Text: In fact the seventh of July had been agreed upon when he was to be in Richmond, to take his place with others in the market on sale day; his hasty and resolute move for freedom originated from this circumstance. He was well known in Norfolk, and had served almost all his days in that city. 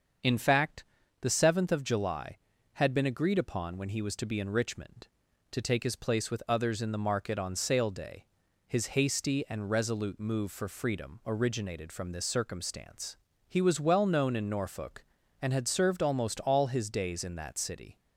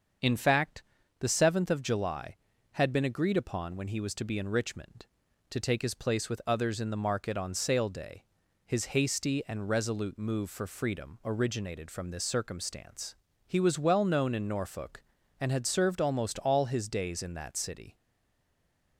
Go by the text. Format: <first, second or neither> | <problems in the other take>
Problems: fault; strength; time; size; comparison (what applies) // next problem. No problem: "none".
first | starts louder than the rest; until 1.5 s; 6.5 dB; also in the first // pauses between "fact" and "the"; slight; at 0.8 s; 0.36 s long; slight in the first // stays silent after the last word; from 17.9 s on; 1.0 s long